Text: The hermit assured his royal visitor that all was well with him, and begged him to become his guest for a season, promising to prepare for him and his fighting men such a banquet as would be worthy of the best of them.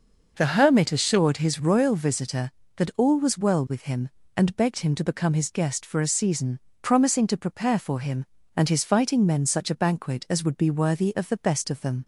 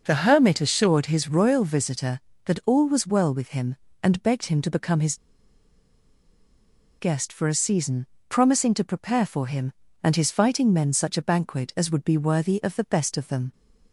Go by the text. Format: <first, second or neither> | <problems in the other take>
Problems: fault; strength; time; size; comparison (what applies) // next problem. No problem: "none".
first | pauses between "his" and "guest"; strong; at 5.1 s; 1.8 s long